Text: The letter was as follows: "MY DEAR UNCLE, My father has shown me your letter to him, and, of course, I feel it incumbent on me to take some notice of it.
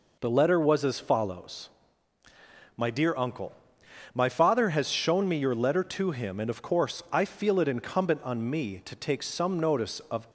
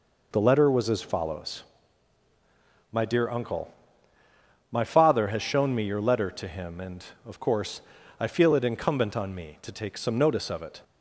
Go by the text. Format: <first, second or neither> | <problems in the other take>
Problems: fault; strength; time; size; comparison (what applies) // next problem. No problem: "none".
second | stops before "it"; at 10.2 s